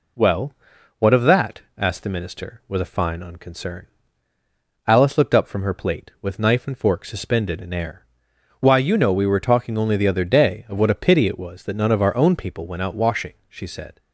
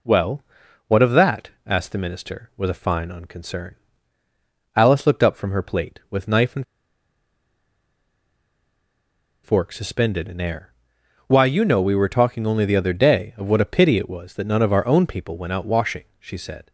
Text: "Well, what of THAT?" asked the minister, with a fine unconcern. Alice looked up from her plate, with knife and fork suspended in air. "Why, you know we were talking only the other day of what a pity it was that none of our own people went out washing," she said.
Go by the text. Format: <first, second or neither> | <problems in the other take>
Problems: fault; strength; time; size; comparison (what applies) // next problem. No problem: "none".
first | pauses between "and" and "fork"; strong; at 6.6 s; 2.7 s long